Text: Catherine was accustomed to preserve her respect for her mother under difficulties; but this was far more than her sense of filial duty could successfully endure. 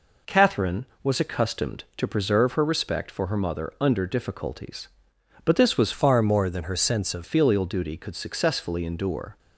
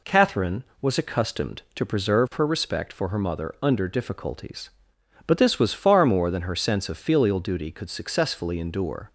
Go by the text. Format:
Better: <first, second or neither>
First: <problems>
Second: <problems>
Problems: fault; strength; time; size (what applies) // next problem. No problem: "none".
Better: second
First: changes voice from "far" to "of"; from 5.9 to 7.2 s; 1.3 s long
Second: none